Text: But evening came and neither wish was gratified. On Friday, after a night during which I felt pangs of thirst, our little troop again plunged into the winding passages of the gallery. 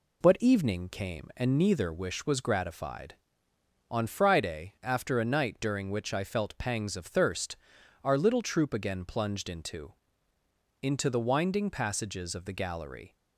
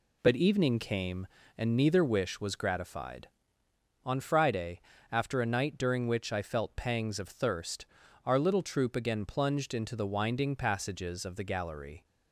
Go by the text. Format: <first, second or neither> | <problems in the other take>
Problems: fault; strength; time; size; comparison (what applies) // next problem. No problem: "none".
second | says "into" twice; at 10.8 s